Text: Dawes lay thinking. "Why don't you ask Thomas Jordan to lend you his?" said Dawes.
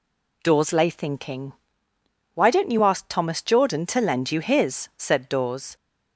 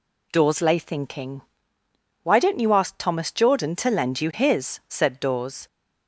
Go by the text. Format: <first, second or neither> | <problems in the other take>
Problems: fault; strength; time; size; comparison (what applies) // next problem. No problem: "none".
neither | none